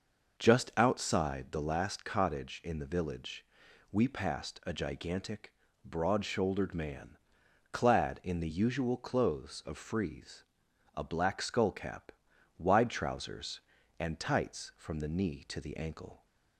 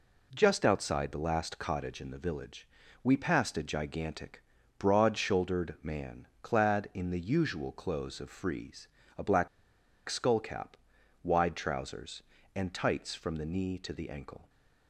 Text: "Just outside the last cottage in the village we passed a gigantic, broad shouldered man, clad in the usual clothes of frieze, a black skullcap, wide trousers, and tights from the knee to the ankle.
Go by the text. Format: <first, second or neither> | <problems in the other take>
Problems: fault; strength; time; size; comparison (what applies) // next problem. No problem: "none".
first | pauses between "village" and "we"; at 2.6 s; 0.38 s long; noticeable in the first // pauses between "black" and "skullcap"; noticeable; at 9.4 s; 0.61 s long